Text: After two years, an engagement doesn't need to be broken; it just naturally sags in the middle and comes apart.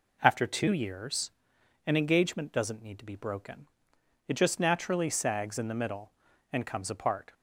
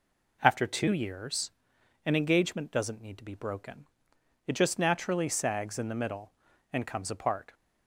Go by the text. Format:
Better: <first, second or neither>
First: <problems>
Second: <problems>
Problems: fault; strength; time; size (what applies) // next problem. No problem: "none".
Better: neither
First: none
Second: none